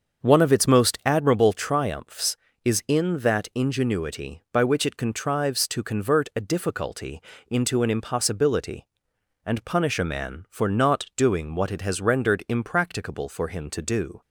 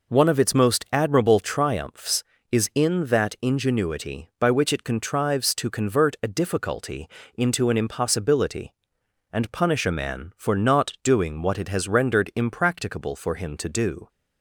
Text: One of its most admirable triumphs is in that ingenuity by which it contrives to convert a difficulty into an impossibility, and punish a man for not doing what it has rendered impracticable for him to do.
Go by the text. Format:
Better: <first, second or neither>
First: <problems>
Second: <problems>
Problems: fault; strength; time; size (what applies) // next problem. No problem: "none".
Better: second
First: starts louder than the rest; until 1.4 s; 6.5 dB // pauses between "difficulty" and "into"; slight; at 7.2 s; 0.26 s long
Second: pauses between "difficulty" and "into"; slight; at 7.0 s; 0.26 s long